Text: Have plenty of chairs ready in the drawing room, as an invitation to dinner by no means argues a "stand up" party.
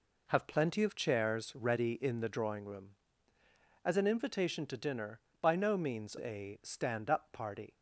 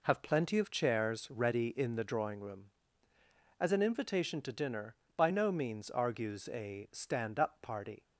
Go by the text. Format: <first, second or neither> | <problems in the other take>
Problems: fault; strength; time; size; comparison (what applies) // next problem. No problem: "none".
second | skips "argues"; at 6.1 s